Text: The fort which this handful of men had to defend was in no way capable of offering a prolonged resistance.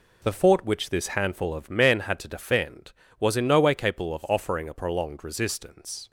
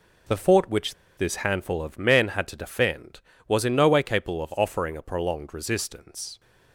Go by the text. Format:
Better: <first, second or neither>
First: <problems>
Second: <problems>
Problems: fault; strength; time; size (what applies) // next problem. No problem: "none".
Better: first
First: none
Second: pauses between "which" and "this"; slight; at 0.9 s; 0.23 s long